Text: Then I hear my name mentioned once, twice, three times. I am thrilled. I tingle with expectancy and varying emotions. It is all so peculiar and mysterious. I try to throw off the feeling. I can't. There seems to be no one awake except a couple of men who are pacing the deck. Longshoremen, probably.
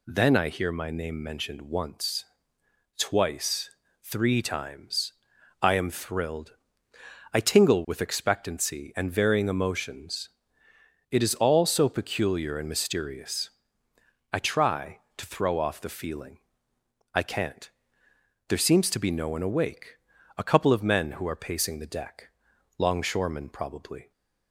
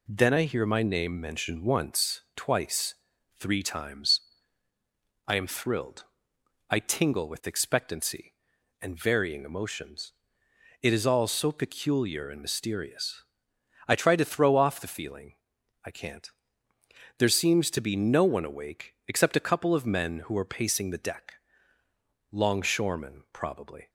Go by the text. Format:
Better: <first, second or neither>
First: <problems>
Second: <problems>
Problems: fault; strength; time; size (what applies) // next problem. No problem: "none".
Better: second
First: skips "except"; at 20.1 s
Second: none